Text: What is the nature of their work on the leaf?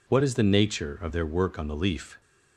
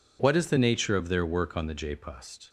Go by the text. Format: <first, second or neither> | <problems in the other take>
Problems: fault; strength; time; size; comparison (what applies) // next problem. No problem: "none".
first | says "jpust" for "leaf"; at 1.7 s